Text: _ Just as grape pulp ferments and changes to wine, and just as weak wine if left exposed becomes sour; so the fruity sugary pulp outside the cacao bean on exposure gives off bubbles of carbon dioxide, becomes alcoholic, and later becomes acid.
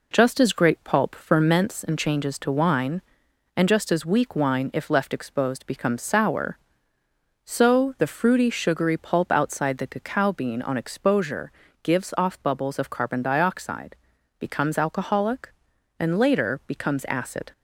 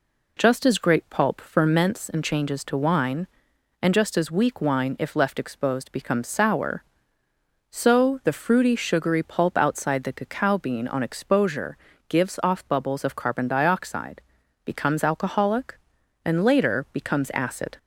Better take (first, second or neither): second